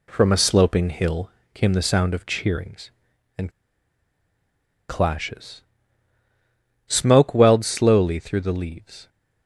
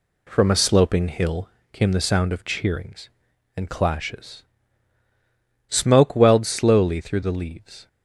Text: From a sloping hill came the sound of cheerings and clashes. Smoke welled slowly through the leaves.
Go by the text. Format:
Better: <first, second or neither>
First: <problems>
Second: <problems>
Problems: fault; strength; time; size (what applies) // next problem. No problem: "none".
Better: second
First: pauses between "hill" and "came"; slight; at 1.3 s; 0.22 s long // pauses between "and" and "clashes"; strong; at 3.4 s; 1.3 s long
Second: pauses between "hill" and "came"; slight; at 1.4 s; 0.22 s long